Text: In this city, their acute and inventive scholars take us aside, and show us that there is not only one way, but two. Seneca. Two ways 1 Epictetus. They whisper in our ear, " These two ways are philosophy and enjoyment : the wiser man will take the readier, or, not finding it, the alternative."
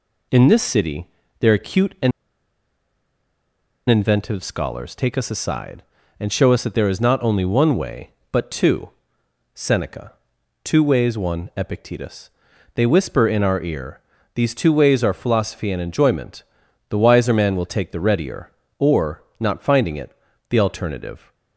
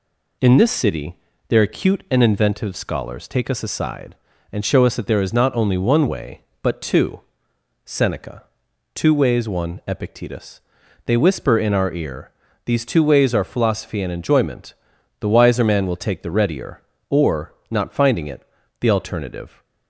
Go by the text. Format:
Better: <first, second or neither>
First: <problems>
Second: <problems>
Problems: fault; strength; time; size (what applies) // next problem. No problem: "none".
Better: second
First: pauses between "and" and "inventive"; strong; at 2.1 s; 1.7 s long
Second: none